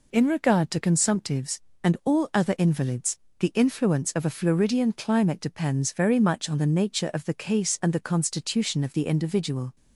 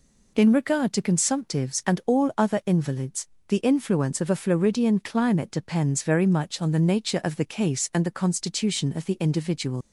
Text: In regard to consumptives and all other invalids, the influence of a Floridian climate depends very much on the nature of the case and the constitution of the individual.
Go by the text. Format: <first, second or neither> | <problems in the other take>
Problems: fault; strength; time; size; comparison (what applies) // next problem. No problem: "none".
first | leaves "individual" unfinished; at 9.8 s; 110 ms